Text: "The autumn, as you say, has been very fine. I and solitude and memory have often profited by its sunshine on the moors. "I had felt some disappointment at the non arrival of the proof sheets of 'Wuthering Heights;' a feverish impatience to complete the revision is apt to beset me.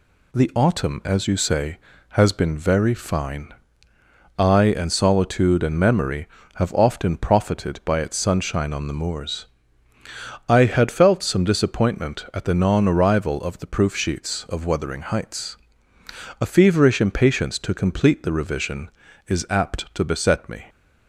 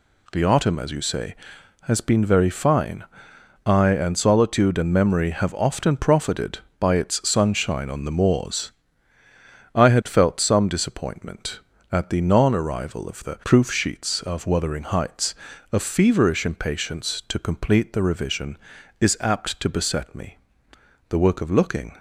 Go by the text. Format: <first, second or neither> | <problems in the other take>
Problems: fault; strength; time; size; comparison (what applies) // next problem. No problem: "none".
first | goes on to say "The work of looking"; noticeable; from 21.0 s on; 0.86 s long